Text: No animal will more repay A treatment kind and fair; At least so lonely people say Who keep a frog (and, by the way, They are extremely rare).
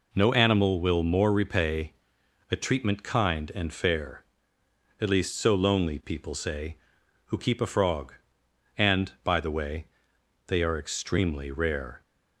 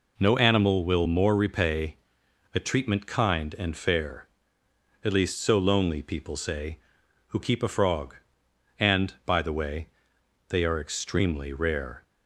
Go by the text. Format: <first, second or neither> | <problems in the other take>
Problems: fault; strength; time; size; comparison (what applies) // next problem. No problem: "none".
neither | pauses between "repay" and "A"; noticeable; the same in both